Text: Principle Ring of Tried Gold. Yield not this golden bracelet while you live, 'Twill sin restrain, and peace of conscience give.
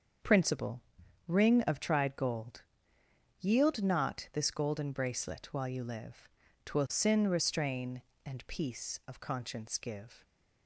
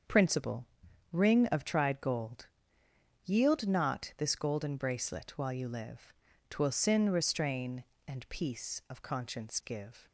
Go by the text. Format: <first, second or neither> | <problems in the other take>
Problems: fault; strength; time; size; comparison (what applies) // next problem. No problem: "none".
neither | starts louder than the rest; the same in both // pauses between "Principle" and "Ring"; noticeable; the same in both